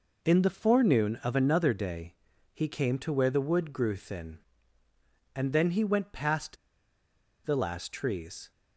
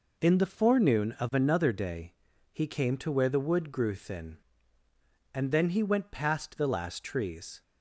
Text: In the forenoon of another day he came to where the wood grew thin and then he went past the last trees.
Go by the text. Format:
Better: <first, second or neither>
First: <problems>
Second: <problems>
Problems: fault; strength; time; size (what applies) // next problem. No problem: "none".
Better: second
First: pauses between "day" and "he"; at 2.1 s; 0.40 s long // pauses between "past" and "the"; noticeable; at 6.5 s; 0.90 s long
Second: pauses between "day" and "he"; at 2.1 s; 0.40 s long